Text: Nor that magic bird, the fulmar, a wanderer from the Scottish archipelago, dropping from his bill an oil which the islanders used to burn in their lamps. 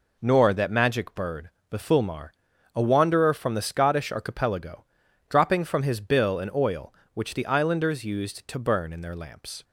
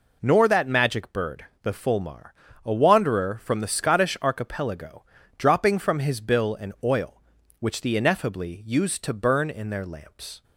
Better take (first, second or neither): first